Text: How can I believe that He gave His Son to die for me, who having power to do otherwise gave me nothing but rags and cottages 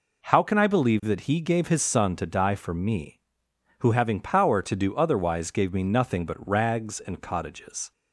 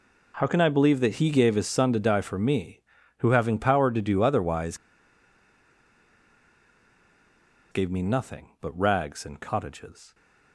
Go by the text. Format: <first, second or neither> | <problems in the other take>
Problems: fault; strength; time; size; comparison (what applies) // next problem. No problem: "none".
first | pauses between "otherwise" and "gave"; strong; at 4.7 s; 2.9 s long